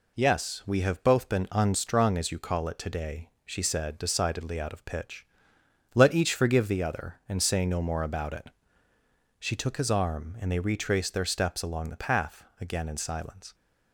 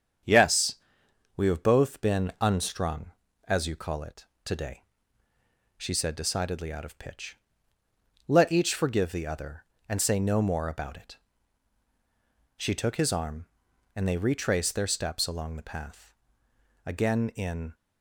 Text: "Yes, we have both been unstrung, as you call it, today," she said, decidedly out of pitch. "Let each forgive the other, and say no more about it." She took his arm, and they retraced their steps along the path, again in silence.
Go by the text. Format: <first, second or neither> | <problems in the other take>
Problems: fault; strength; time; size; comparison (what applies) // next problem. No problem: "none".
first | starts louder than the rest; strong; until 1.8 s; 8 dB // stops before "silence"; at 17.7 s